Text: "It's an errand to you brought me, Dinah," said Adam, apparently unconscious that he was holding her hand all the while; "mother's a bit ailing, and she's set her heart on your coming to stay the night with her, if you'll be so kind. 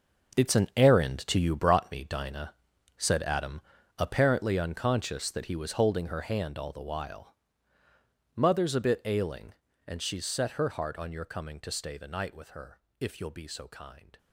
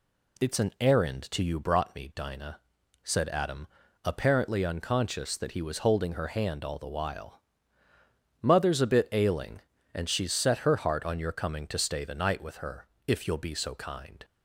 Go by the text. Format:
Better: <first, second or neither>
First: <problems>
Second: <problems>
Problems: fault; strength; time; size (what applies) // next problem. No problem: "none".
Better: second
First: gets quieter; strong; throughout; 13 dB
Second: none